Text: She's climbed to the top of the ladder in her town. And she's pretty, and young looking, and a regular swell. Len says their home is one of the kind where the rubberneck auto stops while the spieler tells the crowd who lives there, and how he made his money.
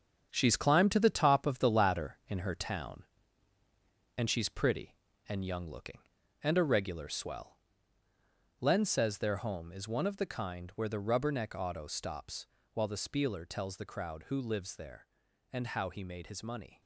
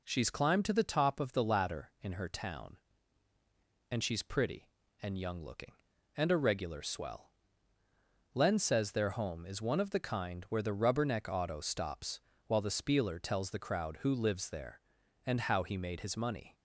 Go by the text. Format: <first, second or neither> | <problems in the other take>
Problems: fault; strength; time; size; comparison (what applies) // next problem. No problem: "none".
second | gets quieter; strong; throughout; 8.5 dB // pauses between "stops" and "while"; slight; at 12.4 s; 0.28 s long; slight in the second